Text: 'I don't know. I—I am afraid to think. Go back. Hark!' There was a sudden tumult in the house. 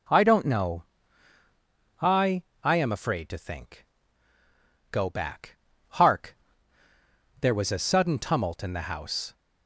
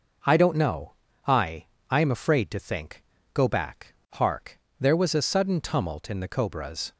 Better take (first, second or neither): first